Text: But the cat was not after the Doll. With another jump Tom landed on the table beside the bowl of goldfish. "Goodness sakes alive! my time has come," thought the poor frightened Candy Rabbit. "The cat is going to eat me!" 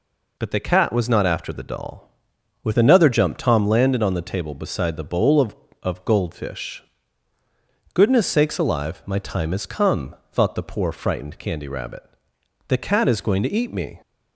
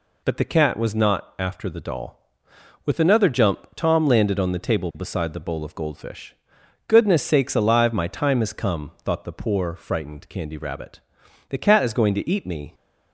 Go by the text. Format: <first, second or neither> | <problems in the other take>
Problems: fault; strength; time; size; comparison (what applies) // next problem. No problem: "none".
second | says "of" twice; at 5.8 s